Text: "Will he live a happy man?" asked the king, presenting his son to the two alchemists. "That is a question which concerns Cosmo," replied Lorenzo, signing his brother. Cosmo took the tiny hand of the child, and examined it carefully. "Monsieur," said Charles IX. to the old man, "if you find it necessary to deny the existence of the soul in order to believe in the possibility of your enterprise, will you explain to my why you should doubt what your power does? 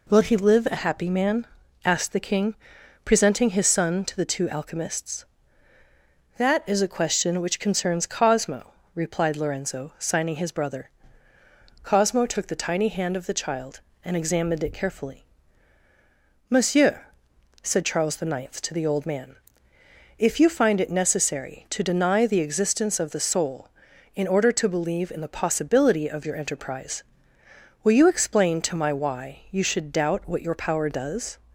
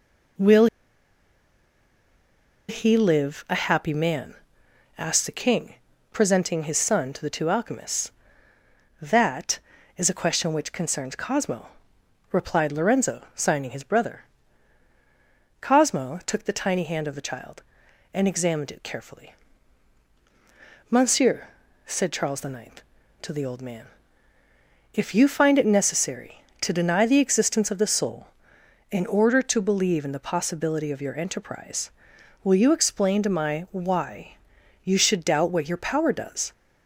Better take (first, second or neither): first